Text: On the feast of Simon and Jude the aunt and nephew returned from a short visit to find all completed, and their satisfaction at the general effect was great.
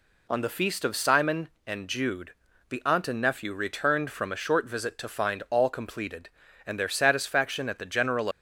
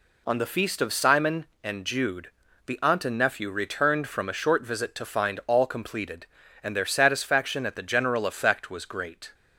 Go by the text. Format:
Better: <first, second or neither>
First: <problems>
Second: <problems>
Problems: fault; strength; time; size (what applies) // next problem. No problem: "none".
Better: second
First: pauses between "Jude" and "the"; slight; at 2.3 s; 0.36 s long // stops before "effect was great"; at 8.3 s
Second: pauses between "Jude" and "the"; slight; at 2.2 s; 0.36 s long